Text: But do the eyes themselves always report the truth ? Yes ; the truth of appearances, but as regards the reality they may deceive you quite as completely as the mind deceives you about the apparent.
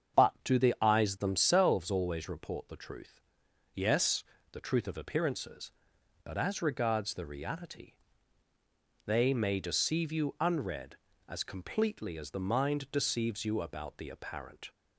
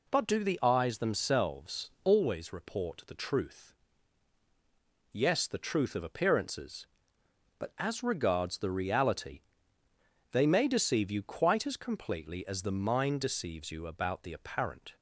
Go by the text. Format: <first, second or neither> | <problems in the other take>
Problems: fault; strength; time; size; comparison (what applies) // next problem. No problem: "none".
second | starts louder than the rest; strong; until 1.3 s; 7.5 dB // pauses between "reality" and "they"; at 7.9 s; 1.1 s long; noticeable in the second // says "unread" for "quite"; at 10.3 s